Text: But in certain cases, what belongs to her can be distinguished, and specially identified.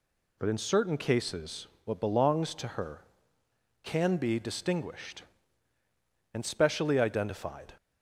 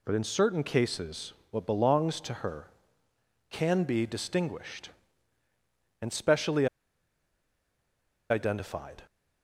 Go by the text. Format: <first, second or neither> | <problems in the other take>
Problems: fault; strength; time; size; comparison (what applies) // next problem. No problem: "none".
first | pauses between "specially" and "identified"; strong; at 6.6 s; 1.6 s long